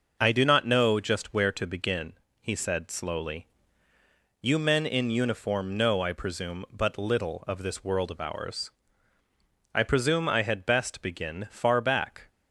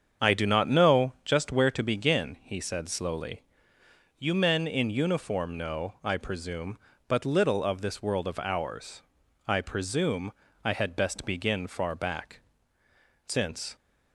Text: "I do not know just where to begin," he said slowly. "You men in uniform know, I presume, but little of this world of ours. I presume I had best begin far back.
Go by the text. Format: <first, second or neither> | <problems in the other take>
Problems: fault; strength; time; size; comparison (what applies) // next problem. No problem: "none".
first | starts louder than the rest; strong; until 1.3 s; 7.5 dB // pauses between "presume" and "I"; slight; at 10.3 s; 0.32 s long // goes on to say "Since"; slight; from 13.2 s on; 0.48 s long